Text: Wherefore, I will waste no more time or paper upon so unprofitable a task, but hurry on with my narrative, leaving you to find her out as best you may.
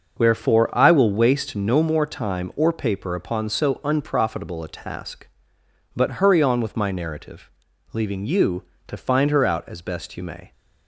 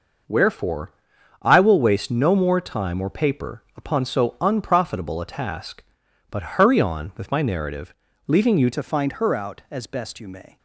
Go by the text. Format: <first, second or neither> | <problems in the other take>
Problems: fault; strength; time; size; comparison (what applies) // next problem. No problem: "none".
first | changes voice at "to"; from 8.7 s on; 1.8 s long